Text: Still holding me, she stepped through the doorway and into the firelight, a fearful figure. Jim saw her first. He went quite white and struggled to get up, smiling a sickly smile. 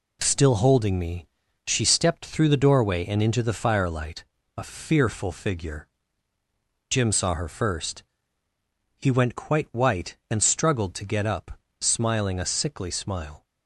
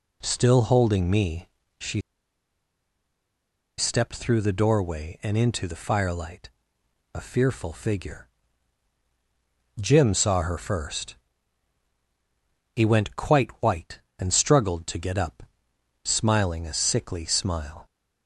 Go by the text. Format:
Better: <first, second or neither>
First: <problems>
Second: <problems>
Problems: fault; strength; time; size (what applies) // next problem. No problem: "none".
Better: first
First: none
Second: pauses between "she" and "stepped"; strong; at 1.9 s; 1.7 s long